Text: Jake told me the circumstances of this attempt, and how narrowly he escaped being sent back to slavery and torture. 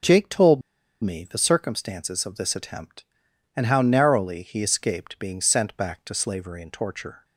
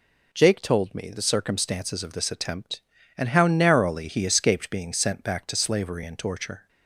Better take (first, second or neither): second